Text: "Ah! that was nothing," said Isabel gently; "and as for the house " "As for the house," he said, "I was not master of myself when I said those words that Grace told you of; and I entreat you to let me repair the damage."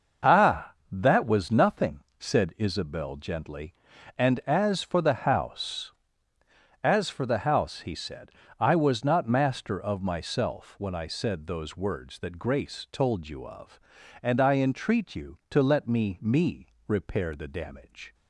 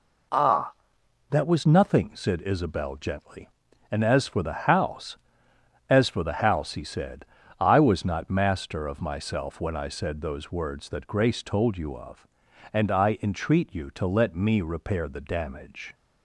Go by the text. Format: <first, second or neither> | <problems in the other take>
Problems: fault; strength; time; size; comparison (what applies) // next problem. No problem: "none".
second | starts louder than the rest; noticeable; until 1.4 s; 6 dB // says "me" twice; at 16.2 s